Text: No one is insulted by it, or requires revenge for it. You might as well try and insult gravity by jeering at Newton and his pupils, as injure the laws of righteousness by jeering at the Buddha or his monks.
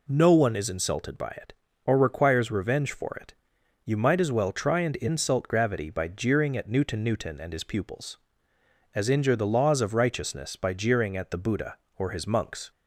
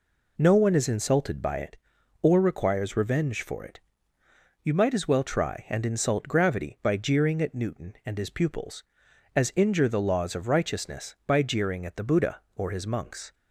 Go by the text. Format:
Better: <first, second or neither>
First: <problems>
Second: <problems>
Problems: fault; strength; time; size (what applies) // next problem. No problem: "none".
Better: second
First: says "Newton" twice; at 7.0 s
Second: none